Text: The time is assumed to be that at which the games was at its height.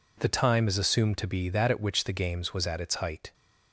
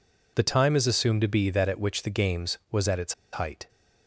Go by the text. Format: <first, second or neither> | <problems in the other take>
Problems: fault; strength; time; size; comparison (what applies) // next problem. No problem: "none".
first | pauses between "its" and "height"; slight; at 3.1 s; 0.19 s long